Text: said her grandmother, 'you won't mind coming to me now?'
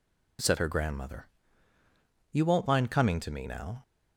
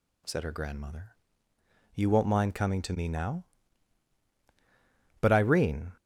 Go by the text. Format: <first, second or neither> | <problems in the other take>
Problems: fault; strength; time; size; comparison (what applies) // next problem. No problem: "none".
first | goes on to say "But Irene"; noticeable; from 5.1 s on; 0.72 s long